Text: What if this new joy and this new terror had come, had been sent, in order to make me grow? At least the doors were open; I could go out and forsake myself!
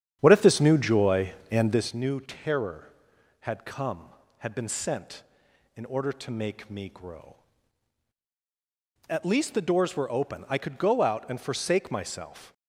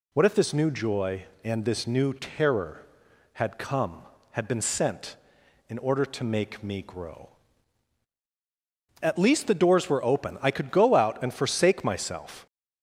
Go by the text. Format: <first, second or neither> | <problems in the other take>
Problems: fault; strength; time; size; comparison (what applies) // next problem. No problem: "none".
second | starts louder than the rest; strong; until 1.9 s; 9 dB